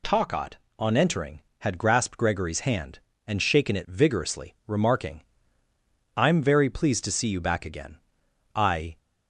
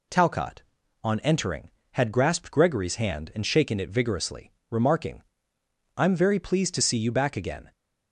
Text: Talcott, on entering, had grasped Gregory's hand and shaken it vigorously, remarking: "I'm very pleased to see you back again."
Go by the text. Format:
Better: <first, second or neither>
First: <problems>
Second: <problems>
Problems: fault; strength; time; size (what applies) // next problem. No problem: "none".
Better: second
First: goes on to say "I"; slight; from 8.5 s on; 0.44 s long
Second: none